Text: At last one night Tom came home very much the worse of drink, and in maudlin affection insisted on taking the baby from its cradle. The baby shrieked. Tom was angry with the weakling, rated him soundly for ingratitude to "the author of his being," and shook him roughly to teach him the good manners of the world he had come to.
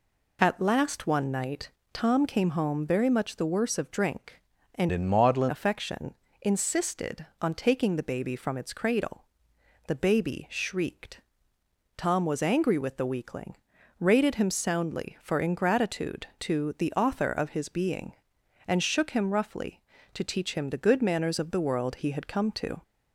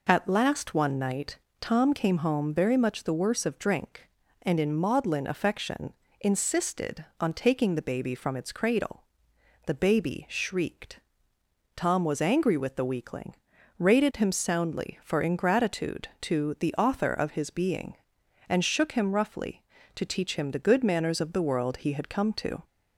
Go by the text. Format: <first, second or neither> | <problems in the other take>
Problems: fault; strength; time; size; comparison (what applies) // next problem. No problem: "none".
second | pauses between "night" and "Tom"; slight; at 1.7 s; 0.22 s long; slight in the second // changes voice from "in" to "maudlin"; from 4.9 to 5.5 s; 0.6 s long // pauses between "affection" and "insisted"; slight; at 6.1 s; 0.30 s long; slight in the second